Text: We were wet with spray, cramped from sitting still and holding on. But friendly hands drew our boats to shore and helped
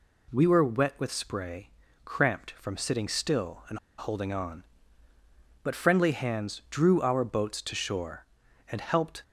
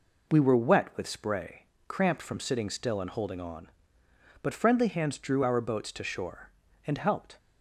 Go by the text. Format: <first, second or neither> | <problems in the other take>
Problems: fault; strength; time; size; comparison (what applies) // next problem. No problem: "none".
second | pauses between "and" and "holding"; slight; at 3.7 s; 0.20 s long